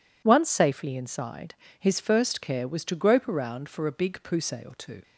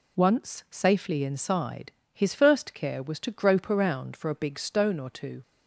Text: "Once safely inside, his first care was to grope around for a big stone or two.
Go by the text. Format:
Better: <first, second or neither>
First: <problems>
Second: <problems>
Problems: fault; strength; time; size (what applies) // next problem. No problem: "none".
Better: second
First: says "pousse" for "stone"; at 4.2 s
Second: none